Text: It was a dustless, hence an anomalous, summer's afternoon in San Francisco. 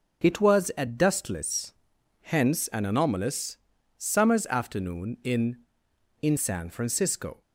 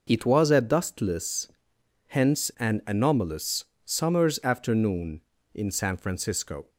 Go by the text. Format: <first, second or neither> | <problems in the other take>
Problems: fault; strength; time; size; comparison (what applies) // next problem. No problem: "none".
second | says "in" twice; at 6.2 s